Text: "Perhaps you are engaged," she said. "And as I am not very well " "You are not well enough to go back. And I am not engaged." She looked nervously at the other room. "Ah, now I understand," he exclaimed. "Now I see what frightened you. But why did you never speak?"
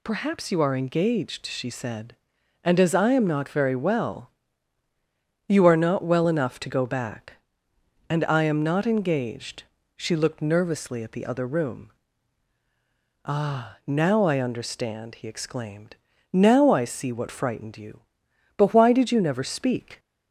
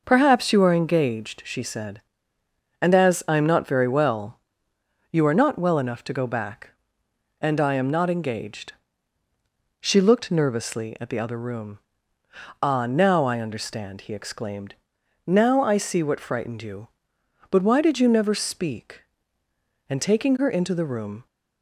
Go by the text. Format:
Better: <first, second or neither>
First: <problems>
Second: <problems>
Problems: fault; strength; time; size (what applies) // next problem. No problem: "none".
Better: first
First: none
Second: goes on to say "And taking her into the room"; from 19.8 s on; 1.3 s long